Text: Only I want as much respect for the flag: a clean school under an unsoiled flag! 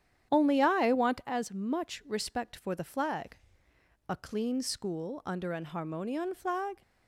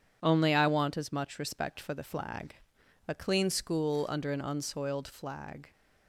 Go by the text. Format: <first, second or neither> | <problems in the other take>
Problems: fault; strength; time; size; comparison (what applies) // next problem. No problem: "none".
second | starts louder than the rest; strong; until 1.3 s; 10 dB // says "harmonion" for "unsoiled"; at 5.6 s